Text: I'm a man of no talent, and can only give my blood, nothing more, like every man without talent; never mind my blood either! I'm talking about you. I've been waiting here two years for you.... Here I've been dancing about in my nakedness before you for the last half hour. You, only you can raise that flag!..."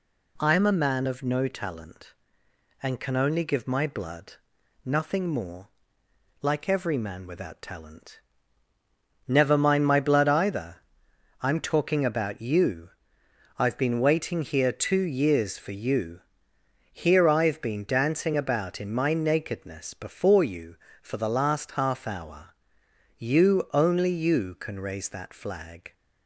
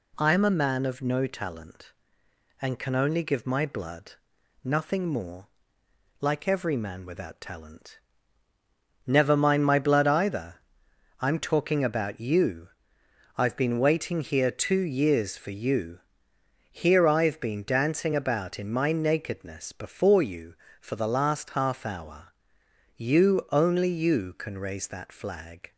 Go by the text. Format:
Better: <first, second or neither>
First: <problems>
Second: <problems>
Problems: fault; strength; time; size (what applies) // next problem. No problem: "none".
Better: neither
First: none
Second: none